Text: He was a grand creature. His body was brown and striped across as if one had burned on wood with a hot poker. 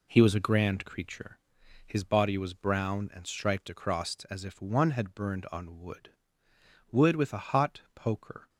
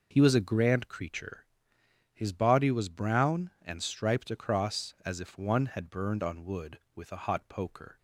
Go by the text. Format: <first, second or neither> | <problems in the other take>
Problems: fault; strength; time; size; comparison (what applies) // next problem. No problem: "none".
second | says "wood" twice; at 6.9 s